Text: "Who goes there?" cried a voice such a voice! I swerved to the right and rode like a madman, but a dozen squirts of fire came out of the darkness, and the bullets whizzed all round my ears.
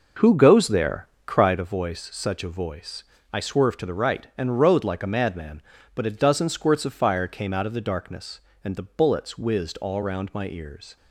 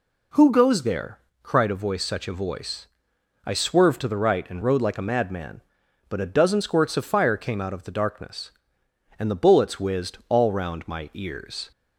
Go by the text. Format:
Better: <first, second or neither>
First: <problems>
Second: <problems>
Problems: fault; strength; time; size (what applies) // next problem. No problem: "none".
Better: second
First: starts louder than the rest; noticeable; until 1.6 s; 5.5 dB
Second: none